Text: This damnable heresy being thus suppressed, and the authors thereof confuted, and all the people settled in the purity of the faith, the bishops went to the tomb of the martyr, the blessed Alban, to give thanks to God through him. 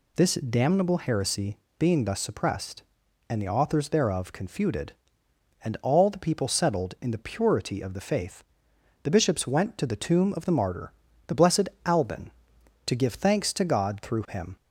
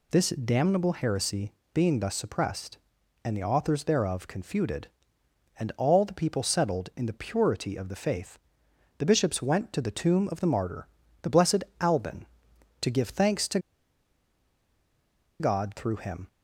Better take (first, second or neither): first